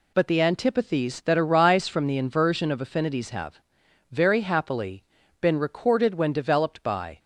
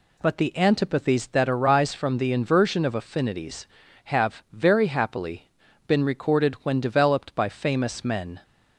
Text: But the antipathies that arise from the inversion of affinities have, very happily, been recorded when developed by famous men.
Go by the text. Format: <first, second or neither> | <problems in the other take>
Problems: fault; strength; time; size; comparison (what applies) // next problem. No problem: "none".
second | stops before "famous men"; at 7.1 s